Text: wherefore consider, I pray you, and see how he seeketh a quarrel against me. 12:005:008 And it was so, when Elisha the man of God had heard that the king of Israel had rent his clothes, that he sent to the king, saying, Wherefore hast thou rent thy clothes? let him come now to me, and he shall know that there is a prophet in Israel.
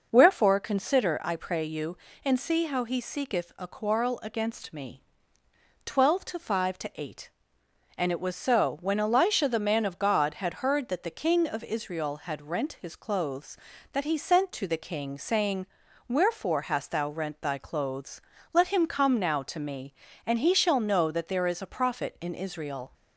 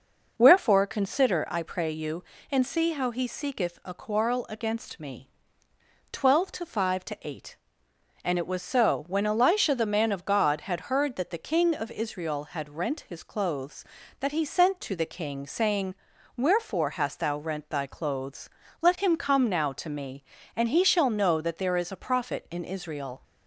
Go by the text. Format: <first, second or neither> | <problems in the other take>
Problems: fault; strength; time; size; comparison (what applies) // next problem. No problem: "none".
neither | none